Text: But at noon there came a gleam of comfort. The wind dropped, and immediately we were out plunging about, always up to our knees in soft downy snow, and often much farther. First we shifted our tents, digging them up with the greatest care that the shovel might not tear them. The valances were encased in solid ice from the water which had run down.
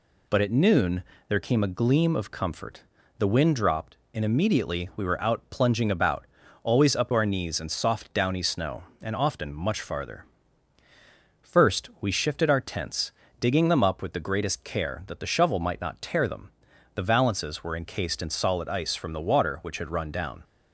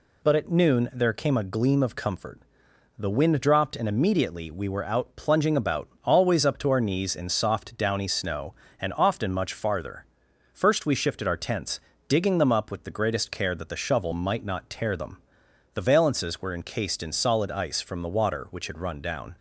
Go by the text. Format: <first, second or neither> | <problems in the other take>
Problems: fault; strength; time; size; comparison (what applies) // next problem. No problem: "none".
second | pauses between "noon" and "there"; slight; at 1.0 s; 0.24 s long // skips "to"; at 7.1 s